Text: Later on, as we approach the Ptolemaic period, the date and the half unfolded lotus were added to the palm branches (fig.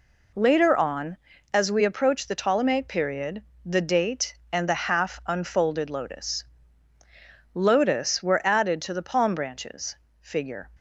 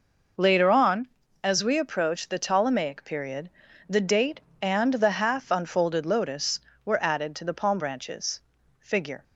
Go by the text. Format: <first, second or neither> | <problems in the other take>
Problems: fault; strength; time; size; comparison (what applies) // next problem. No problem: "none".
second | says "lotus" twice; at 7.5 s